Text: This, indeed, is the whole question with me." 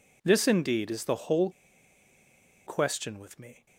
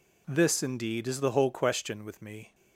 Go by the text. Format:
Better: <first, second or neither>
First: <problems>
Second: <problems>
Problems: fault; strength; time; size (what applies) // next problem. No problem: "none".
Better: second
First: pauses between "whole" and "question"; at 1.4 s; 1.1 s long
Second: none